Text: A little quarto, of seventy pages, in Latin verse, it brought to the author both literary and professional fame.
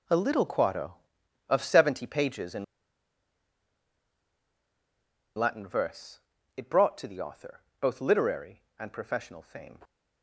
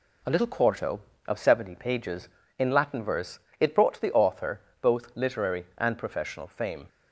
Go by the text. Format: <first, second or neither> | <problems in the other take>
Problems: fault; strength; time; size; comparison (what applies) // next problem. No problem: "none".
second | pauses between "in" and "Latin"; strong; at 2.6 s; 2.7 s long // pauses between "author" and "both"; slight; at 7.6 s; 0.20 s long; slight in the second